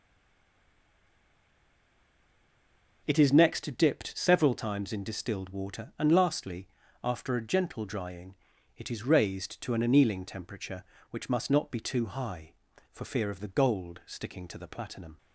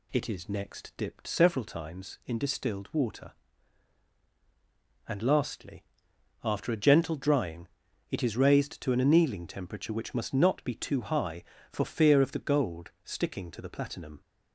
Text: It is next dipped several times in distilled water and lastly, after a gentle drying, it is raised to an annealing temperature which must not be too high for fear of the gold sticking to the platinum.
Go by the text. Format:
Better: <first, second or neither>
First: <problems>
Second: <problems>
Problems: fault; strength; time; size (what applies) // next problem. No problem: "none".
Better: second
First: stays silent before the first word; strong; until 3.0 s; 3.0 s long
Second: none